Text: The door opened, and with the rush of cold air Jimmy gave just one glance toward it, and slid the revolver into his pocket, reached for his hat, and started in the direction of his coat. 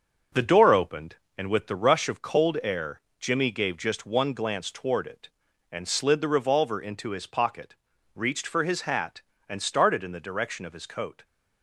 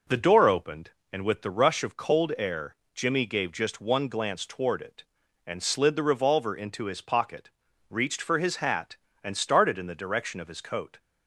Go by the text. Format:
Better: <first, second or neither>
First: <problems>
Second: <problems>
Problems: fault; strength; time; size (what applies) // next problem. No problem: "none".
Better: second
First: gets quieter; noticeable; throughout; 5.5 dB // pauses between "air" and "Jimmy"; slight; at 3.0 s; 0.18 s long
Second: pauses between "air" and "Jimmy"; slight; at 2.7 s; 0.18 s long